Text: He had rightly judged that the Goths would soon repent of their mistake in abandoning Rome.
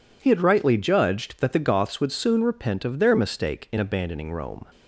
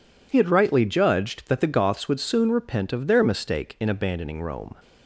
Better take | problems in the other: neither | none

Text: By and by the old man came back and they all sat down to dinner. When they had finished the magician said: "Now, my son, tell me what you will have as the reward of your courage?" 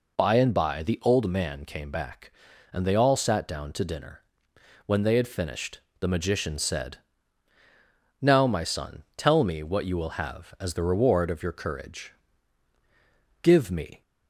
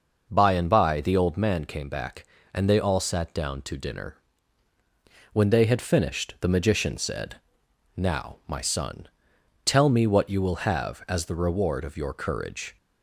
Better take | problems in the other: second | pauses between "finished" and "the"; slight; at 5.7 s; 0.22 s long // goes on to say "Give me"; from 13.4 s on; 0.60 s long

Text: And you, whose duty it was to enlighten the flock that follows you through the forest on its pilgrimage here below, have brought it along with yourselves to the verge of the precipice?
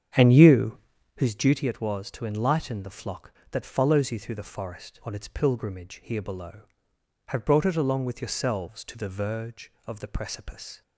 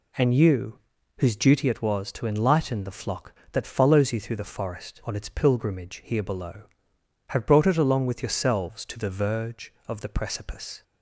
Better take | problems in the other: second | starts louder than the rest; strong; until 1.2 s; 8 dB

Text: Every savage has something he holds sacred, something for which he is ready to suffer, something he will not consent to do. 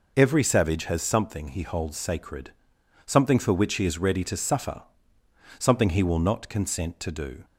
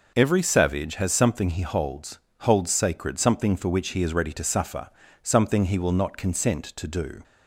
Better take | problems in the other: first | says "holds" twice; at 2.4 s

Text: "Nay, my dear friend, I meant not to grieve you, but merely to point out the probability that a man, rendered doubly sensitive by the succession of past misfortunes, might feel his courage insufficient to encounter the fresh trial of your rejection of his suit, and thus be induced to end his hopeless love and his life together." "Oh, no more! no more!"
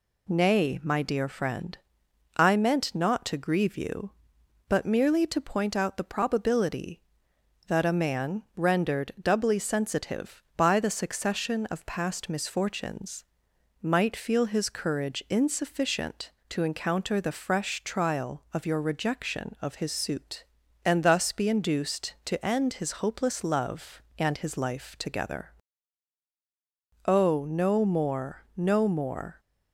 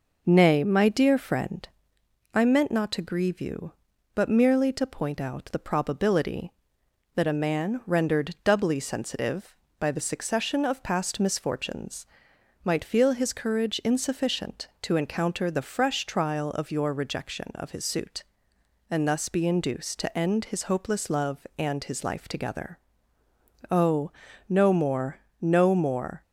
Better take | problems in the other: first | starts louder than the rest; noticeable; until 2.1 s; 5 dB

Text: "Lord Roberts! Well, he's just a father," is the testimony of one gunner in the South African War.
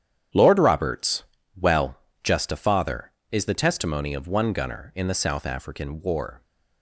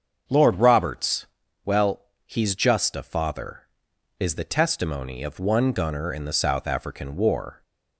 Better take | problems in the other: second | starts louder than the rest; strong; until 1.6 s; 9.5 dB; also in the second // skips "he's"; at 2.0 s

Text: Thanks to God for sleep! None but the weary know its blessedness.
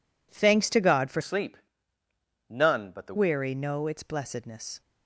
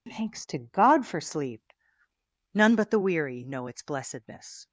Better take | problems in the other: second | changes voice from "sleep" to "the"; from 1.2 to 3.1 s; 1.9 s long

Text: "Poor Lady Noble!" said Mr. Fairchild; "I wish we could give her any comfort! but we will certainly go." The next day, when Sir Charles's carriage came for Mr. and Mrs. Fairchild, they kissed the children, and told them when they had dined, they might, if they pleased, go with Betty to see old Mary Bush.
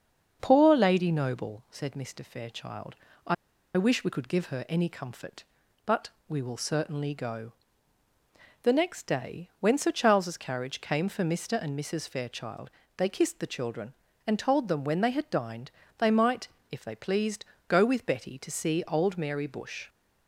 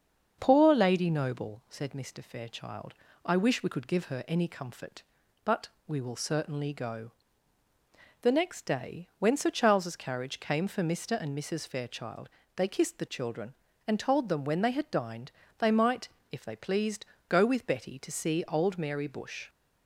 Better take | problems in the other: second | starts louder than the rest; until 1.4 s; 6.5 dB; also in the second // pauses between "I" and "wish"; at 3.3 s; 0.41 s long // pauses between "but" and "we"; slight; at 6.0 s; 0.18 s long; slight in the second

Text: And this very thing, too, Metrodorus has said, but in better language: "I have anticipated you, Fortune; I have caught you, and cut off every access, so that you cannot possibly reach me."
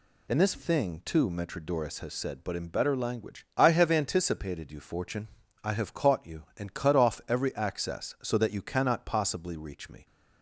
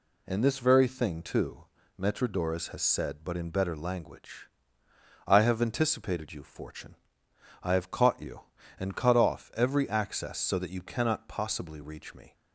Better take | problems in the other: second | skips "very"; at 0.5 s

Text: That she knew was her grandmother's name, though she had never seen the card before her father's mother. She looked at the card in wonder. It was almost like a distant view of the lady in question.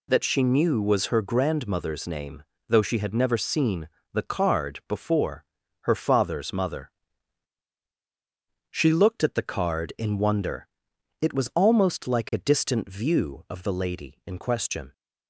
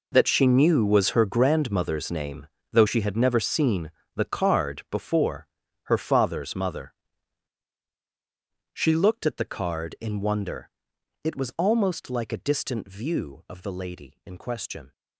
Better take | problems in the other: first | gets quieter; strong; throughout; 15 dB // pauses between "seen" and "the"; slight; at 3.8 s; 0.24 s long; slight in the first // pauses between "before" and "her"; slight; at 5.4 s; 0.36 s long; slight in the first

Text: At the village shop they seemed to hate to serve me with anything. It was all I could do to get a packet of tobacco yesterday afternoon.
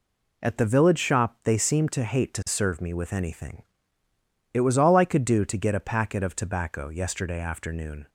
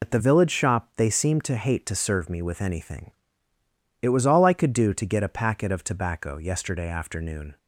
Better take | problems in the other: first | loses the start of "At"; at 0.0 s; 75 ms

